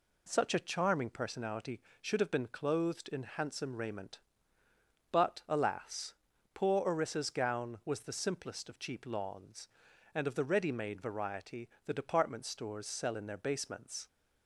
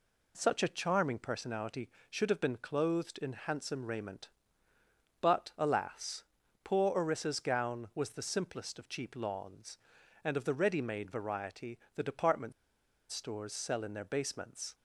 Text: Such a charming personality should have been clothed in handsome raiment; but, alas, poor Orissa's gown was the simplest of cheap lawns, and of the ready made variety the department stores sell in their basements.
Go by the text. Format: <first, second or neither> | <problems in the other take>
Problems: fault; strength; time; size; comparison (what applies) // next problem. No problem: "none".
first | pauses between "variety" and "the"; slight; at 11.7 s; 0.16 s long; slight in the first // pauses between "department" and "stores"; noticeable; at 12.5 s; 0.57 s long